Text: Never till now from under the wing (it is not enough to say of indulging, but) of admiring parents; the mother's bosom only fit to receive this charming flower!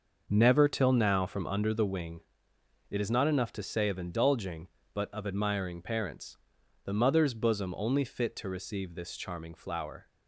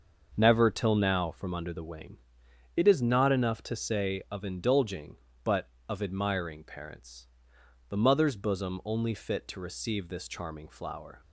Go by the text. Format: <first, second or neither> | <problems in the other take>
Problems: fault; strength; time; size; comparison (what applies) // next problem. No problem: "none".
neither | starts louder than the rest; the same in both